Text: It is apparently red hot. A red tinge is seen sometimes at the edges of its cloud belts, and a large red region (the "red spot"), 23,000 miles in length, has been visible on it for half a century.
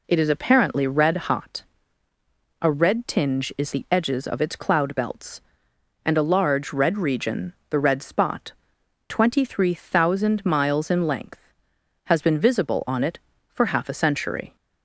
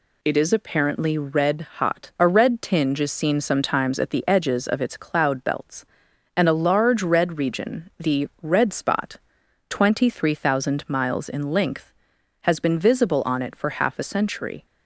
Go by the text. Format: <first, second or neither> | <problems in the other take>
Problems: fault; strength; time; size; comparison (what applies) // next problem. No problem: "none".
second | skips "seen sometimes at"; at 3.7 s